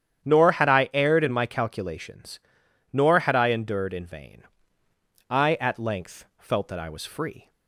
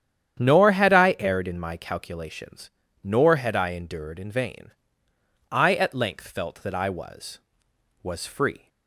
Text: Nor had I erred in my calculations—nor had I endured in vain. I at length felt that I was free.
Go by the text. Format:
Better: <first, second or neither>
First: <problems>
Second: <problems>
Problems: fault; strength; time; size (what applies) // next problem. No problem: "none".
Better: first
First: starts louder than the rest; strong; until 1.3 s; 9 dB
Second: starts louder than the rest; strong; until 1.3 s; 9.5 dB // says "was" twice; at 8.0 s